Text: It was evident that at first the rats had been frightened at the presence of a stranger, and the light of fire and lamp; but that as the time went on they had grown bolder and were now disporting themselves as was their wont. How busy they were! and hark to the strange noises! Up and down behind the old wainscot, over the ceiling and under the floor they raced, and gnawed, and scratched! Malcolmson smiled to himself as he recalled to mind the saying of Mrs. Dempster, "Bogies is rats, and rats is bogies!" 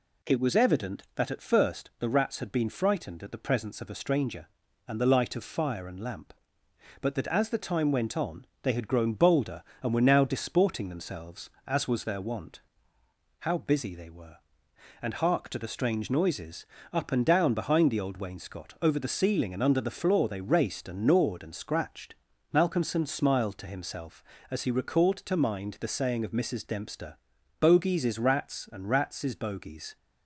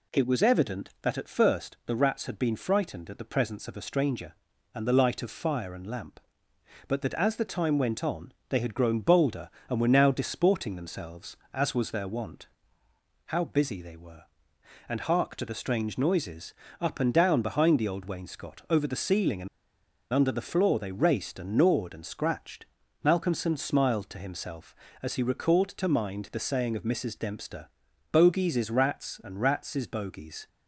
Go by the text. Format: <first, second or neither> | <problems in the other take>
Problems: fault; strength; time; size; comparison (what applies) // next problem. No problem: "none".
first | pauses between "on" and "they"; slight; at 8.3 s; 0.16 s long; slight in the first // pauses between "and" and "under"; noticeable; at 19.4 s; 0.65 s long